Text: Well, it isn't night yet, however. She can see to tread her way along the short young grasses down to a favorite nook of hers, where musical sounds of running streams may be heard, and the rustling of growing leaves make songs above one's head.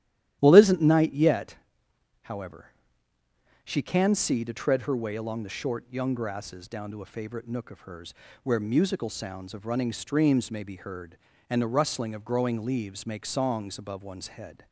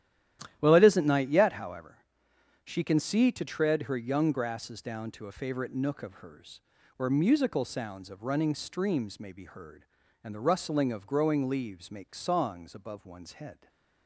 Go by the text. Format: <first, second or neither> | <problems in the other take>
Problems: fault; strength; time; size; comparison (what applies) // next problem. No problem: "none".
first | starts louder than the rest; strong; until 1.6 s; 12.5 dB; strong in the first // skips "way along the short"; at 3.9 s // stays silent after the last word; slight; from 13.5 s on; 0.5 s long